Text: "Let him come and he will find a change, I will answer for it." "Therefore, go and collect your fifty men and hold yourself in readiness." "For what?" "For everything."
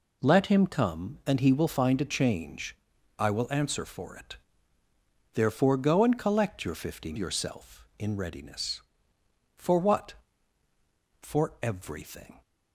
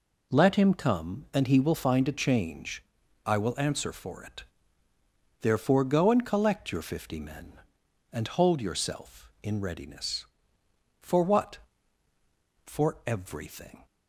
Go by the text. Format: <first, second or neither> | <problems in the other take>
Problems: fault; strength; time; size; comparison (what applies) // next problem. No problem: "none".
second | skips "men and hold"; at 7.1 s